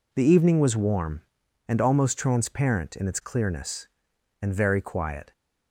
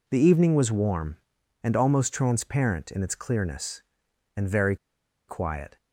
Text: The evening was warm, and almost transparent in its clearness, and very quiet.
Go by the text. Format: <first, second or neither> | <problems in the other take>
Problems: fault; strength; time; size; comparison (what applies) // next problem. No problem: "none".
first | pauses between "very" and "quiet"; noticeable; at 4.7 s; 0.51 s long